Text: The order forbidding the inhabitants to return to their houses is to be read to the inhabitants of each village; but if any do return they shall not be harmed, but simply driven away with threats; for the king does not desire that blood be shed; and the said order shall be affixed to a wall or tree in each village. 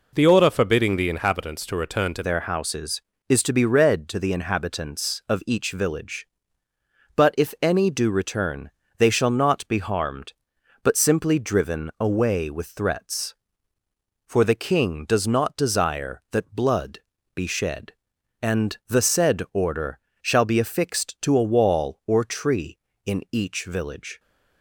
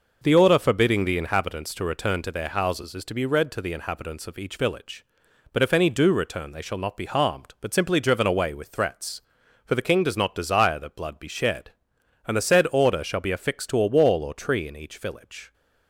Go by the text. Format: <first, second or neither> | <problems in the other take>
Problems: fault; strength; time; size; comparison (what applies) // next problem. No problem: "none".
second | changes voice at "their"; from 2.2 s on; 21.9 s long // pauses between "return" and "they"; slight; at 8.6 s; 0.28 s long // pauses between "blood" and "be"; slight; at 16.9 s; 0.36 s long // pauses between "order" and "shall"; slight; at 19.9 s; 0.22 s long